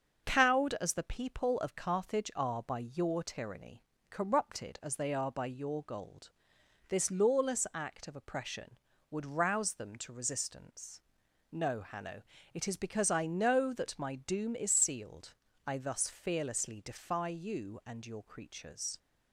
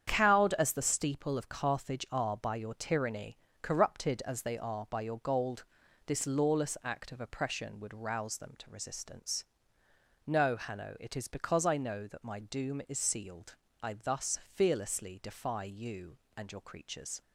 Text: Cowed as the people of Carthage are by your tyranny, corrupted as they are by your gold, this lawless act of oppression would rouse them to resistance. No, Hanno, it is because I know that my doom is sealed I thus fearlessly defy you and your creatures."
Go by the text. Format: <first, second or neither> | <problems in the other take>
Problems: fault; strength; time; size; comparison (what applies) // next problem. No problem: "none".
first | starts louder than the rest; strong; until 1.1 s; 8.5 dB; also in the first // says "steeple" for "people"; at 0.8 s // pauses between "sealed" and "I"; slight; at 13.5 s; 0.26 s long; slight in the first // pauses between "thus" and "fearlessly"; slight; at 14.3 s; 0.16 s long